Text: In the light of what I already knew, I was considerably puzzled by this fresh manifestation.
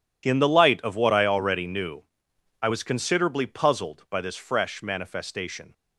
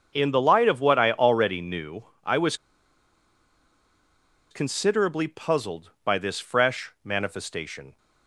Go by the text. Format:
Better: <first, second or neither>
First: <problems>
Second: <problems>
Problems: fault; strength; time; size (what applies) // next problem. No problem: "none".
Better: first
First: none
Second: starts louder than the rest; until 1.1 s; 7 dB // pauses between "was" and "considerably"; strong; at 2.5 s; 1.9 s long